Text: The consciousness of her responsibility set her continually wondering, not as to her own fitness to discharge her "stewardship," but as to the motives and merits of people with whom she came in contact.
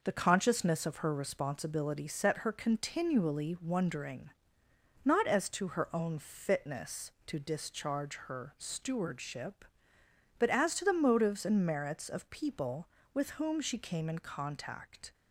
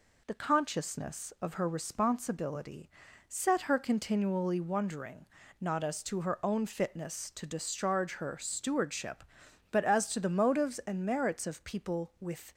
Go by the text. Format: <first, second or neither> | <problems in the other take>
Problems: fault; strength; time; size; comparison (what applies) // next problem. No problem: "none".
first | pauses between "responsibility" and "set"; at 2.8 s; 0.38 s long // stops before "whom she came in contact"; at 12.5 s